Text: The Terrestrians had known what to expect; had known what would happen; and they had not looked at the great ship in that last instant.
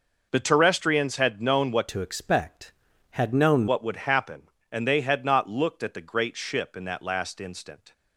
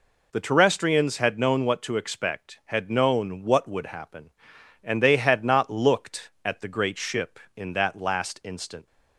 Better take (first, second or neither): second